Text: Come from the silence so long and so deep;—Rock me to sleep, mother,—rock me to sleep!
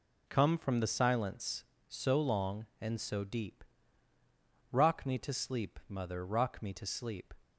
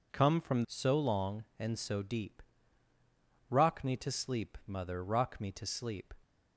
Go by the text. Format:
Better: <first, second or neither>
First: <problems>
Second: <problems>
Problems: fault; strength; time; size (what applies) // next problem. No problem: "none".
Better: first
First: none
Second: skips "the silence"; at 0.6 s